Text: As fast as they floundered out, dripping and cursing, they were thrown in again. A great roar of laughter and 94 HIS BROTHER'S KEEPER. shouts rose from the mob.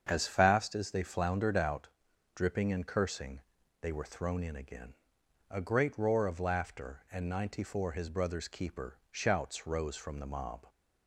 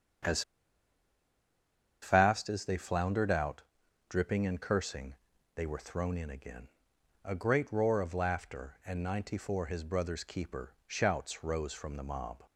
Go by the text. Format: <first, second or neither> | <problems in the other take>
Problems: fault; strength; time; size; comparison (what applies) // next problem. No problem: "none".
first | starts louder than the rest; strong; until 2.8 s; 7.5 dB; strong in the first // pauses between "As" and "fast"; strong; at 0.4 s; 1.6 s long